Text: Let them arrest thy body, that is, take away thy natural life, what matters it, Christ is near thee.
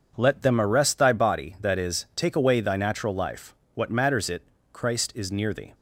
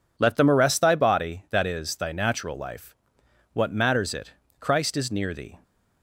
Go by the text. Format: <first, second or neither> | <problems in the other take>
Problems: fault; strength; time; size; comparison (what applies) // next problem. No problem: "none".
first | skips "take away"; at 1.9 s